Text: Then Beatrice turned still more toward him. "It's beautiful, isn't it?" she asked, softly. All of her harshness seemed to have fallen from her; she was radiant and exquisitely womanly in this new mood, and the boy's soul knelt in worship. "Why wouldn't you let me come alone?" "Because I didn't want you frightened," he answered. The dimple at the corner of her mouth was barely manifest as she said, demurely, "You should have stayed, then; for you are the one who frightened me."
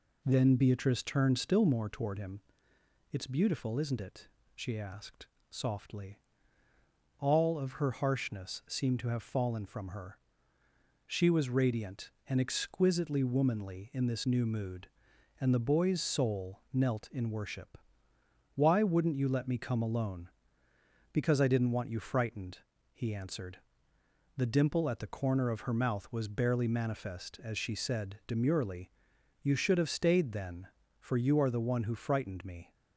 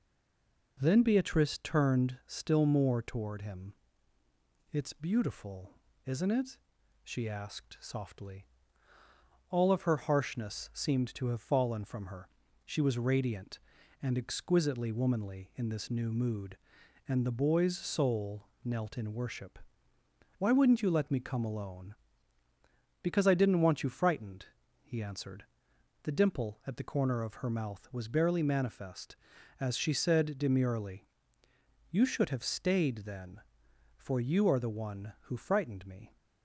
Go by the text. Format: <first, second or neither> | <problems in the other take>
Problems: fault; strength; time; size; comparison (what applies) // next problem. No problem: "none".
first | stays silent before the first word; slight; until 0.7 s; 0.7 s long // pauses between "soul" and "knelt"; slight; at 18.4 s; 0.16 s long